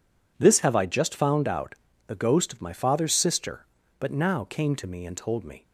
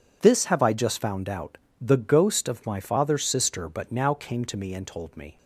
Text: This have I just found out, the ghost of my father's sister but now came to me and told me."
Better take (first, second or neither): neither